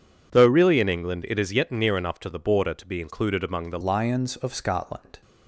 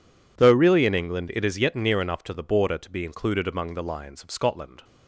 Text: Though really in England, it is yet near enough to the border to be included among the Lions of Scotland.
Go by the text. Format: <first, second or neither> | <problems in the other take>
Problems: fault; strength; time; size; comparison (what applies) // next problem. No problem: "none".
second | changes voice at "Lions"; from 3.8 s on; 1.4 s long